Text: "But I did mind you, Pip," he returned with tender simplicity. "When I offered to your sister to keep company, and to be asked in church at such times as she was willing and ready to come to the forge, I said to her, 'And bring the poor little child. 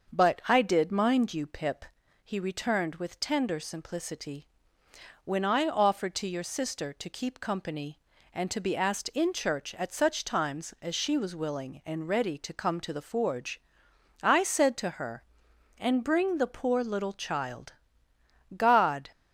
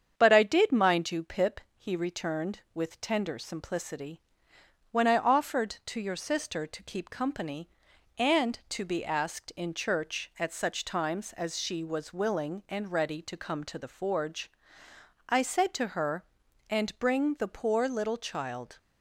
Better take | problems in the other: second | starts louder than the rest; until 1.2 s; 6.5 dB; strong in the second // goes on to say "God"; from 18.5 s on; 0.54 s long

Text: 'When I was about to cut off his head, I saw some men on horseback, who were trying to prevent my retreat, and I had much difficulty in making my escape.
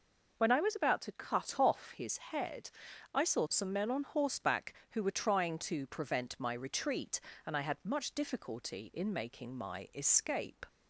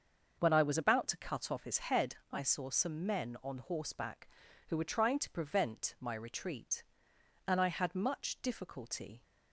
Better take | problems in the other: first | starts louder than the rest; until 1.4 s; 6.5 dB // stops before "in making my escape"; at 9.2 s

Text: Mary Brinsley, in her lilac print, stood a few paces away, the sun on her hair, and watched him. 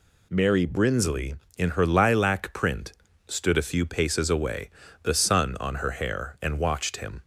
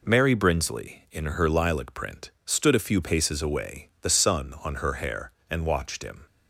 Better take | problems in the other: neither | none

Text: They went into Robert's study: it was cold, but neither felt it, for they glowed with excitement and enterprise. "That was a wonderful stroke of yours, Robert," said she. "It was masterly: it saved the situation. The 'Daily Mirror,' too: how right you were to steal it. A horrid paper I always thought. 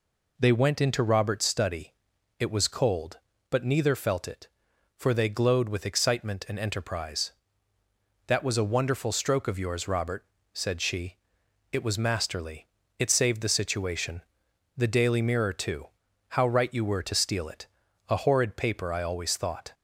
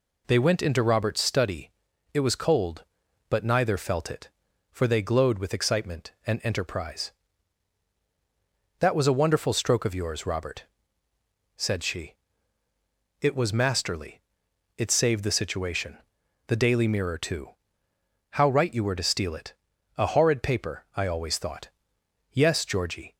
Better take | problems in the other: first | goes on to say "Yes Georgie"; noticeable; from 22.3 s on; 0.82 s long

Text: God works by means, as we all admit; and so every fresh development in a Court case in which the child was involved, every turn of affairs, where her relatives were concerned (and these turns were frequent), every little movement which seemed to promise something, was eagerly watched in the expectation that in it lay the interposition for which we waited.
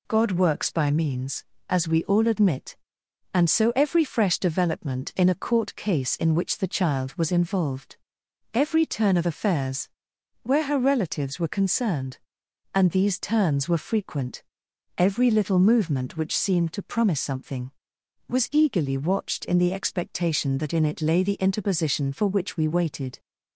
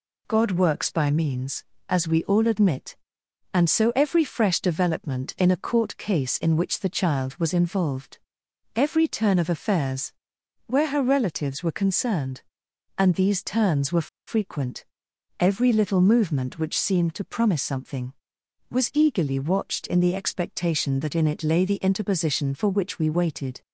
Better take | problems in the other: first | pauses between "were" and "frequent"; slight; at 14.0 s; 0.20 s long

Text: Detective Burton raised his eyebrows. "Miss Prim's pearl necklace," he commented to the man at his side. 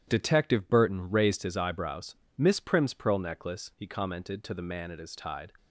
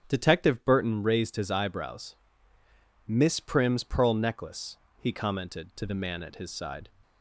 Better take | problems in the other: second | starts louder than the rest; strong; until 1.0 s; 11 dB; strong in the second // says "tide" for "side"; at 5.1 s

